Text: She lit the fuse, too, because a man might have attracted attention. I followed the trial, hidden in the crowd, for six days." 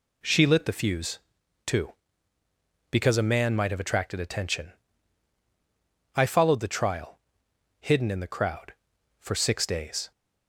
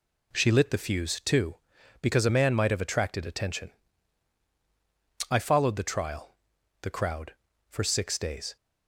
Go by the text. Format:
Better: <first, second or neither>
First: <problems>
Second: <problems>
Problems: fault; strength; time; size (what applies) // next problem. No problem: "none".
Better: first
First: none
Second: skips "hidden in"; at 6.5 s